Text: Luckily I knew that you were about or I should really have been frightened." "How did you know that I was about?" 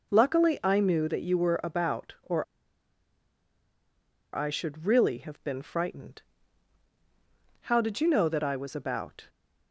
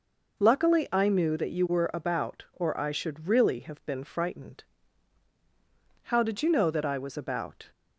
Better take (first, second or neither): second